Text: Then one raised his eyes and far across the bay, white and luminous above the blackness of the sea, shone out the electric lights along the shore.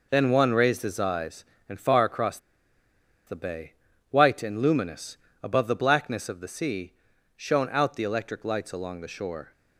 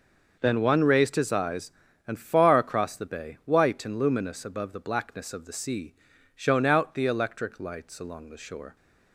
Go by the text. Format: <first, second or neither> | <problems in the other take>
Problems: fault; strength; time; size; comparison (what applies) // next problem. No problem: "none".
second | pauses between "across" and "the"; noticeable; at 2.3 s; 0.89 s long // pauses between "luminous" and "above"; slight; at 5.1 s; 0.26 s long